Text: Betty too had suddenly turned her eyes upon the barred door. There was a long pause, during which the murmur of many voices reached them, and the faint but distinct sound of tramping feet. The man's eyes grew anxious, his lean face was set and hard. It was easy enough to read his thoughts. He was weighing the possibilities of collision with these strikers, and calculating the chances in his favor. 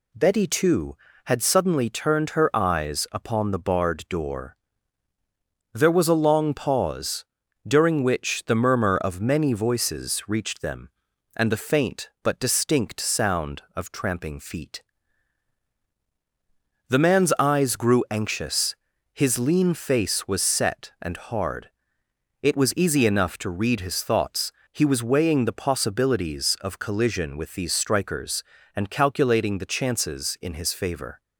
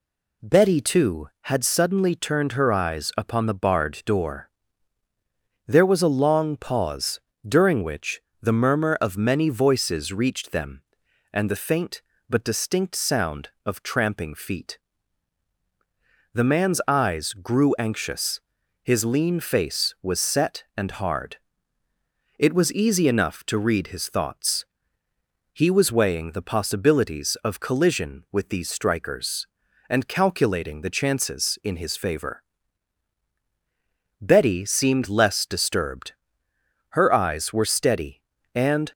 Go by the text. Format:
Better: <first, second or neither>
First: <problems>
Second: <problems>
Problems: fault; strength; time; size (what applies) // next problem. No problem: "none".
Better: first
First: none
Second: pauses between "which" and "the"; slight; at 8.1 s; 0.20 s long // goes on to say "Betty seemed less disturbed Her eyes were steady and"; strong; from 34.2 s on; 4.7 s long